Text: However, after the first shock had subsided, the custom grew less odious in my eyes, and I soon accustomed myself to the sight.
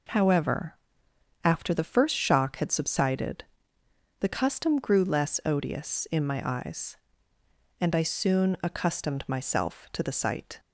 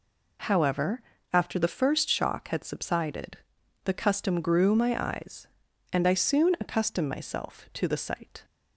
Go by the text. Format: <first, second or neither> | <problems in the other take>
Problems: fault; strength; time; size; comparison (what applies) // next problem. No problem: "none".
first | skips "less odious in"; at 4.7 s